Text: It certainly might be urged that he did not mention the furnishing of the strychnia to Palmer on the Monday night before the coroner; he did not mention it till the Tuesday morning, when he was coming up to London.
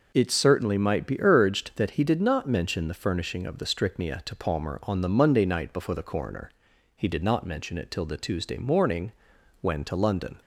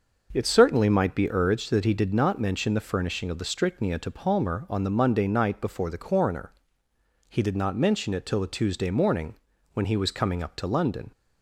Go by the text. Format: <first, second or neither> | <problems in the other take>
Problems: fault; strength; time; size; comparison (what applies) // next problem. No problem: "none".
second | skips "he was coming up"; at 9.8 s